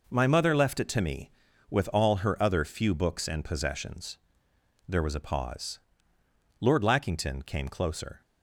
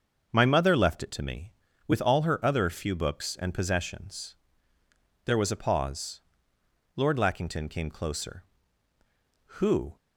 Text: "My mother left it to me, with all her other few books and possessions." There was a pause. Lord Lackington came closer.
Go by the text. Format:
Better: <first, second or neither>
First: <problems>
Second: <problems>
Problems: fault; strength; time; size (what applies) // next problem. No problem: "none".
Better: first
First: none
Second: starts louder than the rest; until 1.3 s; 6 dB // goes on to say "Who"; slight; from 9.6 s on; 0.34 s long